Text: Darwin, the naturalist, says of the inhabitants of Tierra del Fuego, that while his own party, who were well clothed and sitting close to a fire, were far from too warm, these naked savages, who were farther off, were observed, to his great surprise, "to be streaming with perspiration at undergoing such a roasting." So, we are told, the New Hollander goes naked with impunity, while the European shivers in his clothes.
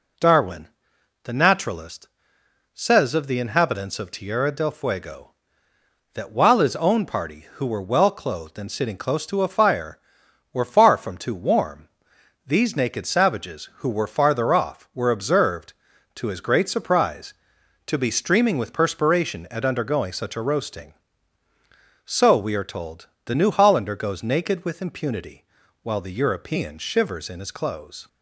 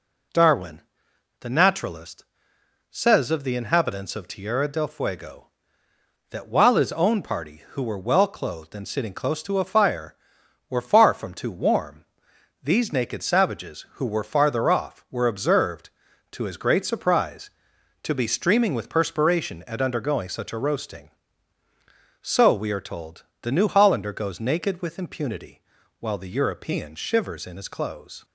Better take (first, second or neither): neither